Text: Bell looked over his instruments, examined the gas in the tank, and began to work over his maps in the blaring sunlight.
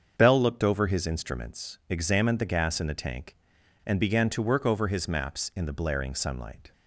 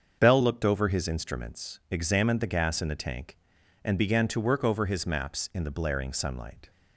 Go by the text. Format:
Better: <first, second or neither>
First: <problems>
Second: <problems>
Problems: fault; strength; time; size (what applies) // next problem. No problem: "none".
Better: neither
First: starts louder than the rest; until 1.1 s; 7 dB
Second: starts louder than the rest; until 1.2 s; 7 dB